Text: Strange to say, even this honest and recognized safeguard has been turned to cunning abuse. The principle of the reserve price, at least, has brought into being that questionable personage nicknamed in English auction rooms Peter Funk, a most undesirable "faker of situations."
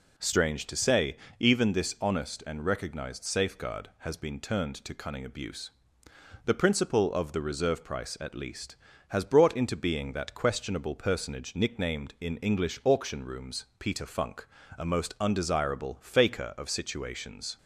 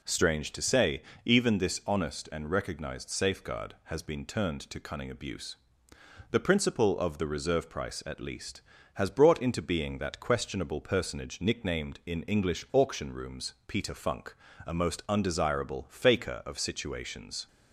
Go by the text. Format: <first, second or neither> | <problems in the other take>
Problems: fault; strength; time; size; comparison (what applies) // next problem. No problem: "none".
neither | none